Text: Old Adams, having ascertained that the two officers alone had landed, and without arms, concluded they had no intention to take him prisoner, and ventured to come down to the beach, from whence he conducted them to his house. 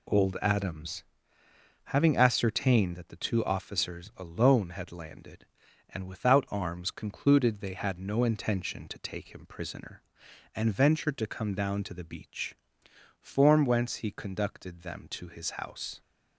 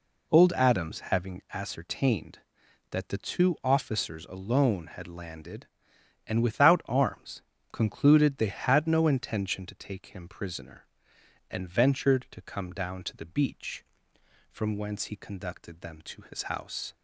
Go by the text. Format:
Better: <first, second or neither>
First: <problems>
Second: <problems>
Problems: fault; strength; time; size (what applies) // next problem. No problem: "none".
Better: second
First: says "form" for "from"; at 13.2 s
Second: none